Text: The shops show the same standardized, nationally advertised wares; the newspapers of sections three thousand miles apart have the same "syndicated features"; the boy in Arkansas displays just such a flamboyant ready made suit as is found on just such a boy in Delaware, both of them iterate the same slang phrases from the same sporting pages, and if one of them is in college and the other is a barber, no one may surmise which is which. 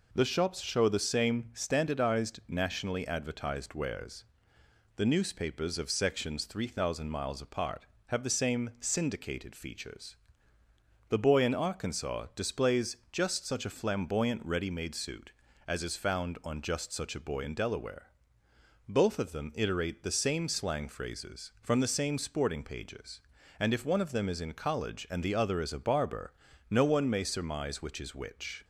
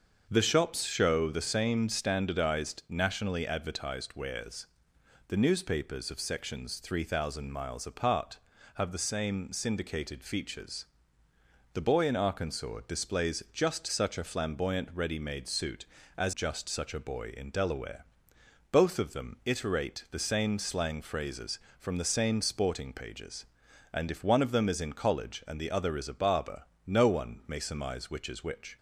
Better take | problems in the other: first | starts louder than the rest; until 1.3 s; 6.5 dB // skips "is found on"; at 16.3 s

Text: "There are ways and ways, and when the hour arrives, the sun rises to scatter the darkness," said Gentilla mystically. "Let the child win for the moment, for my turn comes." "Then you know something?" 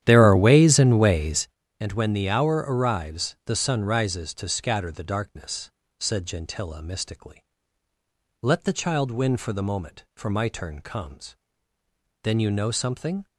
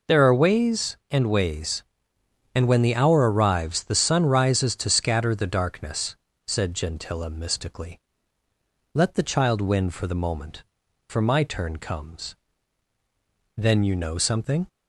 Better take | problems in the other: second | starts louder than the rest; strong; until 1.5 s; 11 dB

